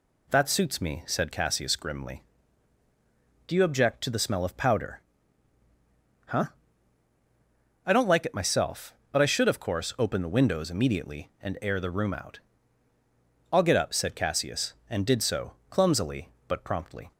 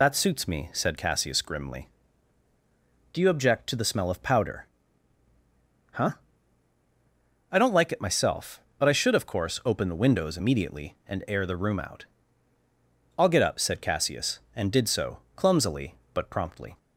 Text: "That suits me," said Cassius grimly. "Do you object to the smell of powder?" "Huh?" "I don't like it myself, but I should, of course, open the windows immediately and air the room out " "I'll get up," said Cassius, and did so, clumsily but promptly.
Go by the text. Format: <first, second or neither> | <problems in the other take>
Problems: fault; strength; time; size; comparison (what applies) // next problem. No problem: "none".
first | loses the start of "That"; at 0.0 s; 45 ms